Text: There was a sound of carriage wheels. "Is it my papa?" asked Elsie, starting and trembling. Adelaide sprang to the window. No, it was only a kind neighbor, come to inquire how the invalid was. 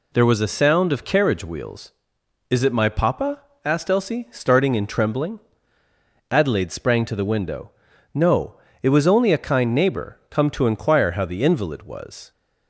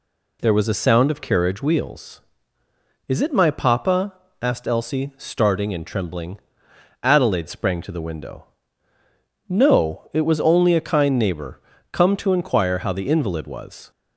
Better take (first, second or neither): neither